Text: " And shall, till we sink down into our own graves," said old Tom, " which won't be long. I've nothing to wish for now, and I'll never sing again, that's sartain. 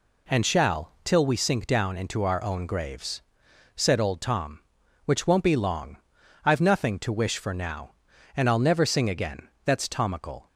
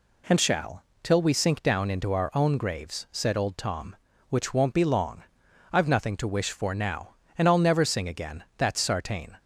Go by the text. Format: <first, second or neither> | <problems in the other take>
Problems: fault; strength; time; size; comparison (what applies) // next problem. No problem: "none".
second | says "tomical" for "sartain"; at 9.8 s